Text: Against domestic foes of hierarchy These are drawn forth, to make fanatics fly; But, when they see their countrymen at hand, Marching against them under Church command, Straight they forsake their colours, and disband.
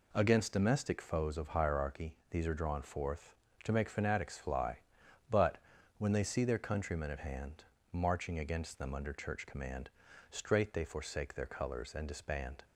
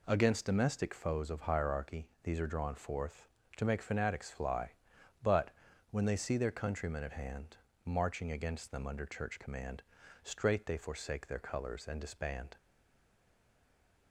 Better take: first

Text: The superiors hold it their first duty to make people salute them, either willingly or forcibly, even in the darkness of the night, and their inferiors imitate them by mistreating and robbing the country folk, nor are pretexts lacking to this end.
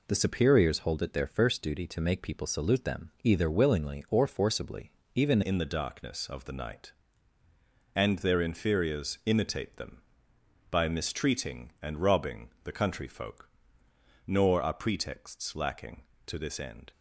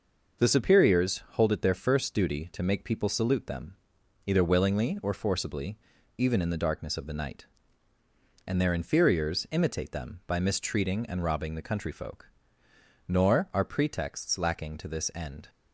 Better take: second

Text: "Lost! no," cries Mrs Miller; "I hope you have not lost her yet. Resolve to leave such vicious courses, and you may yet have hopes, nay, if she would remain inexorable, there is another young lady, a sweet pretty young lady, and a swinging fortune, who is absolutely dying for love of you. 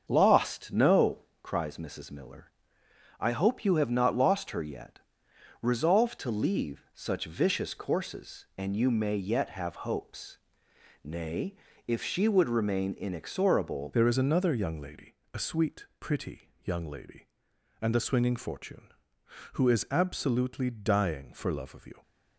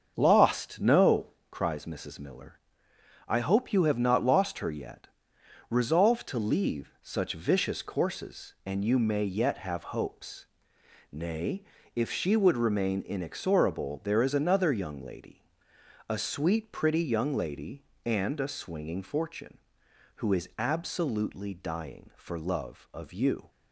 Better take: second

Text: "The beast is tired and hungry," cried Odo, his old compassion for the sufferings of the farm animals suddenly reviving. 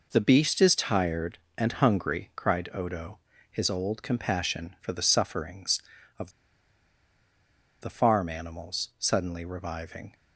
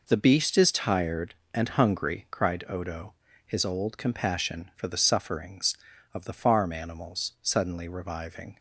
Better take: second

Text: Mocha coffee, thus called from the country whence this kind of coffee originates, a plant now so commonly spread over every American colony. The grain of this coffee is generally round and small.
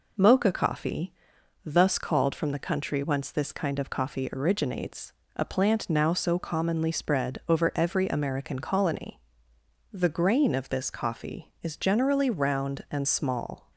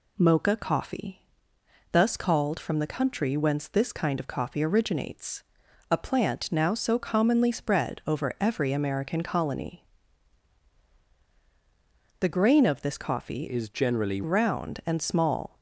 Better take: first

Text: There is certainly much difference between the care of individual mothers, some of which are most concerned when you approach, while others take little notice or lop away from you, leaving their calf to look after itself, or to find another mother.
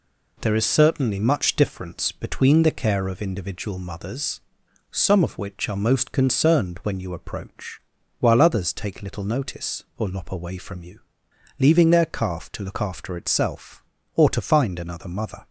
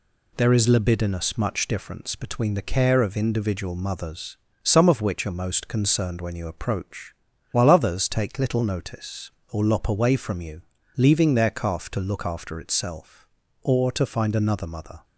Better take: first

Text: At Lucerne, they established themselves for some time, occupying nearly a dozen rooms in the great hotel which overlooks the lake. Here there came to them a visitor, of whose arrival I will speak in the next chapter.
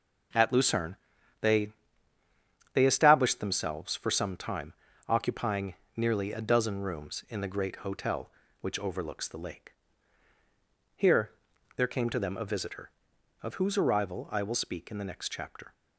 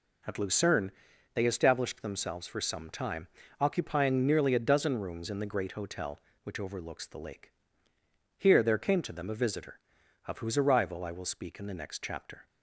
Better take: second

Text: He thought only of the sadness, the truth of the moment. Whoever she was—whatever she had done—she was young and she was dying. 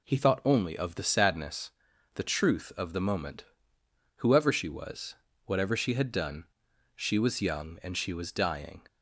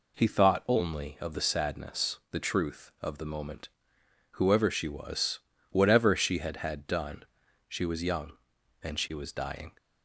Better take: first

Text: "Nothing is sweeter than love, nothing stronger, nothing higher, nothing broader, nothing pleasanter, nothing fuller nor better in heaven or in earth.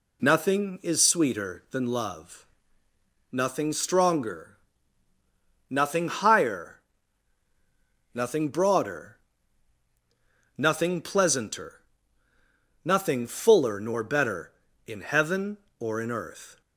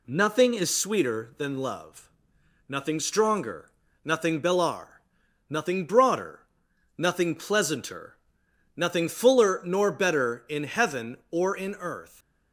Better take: first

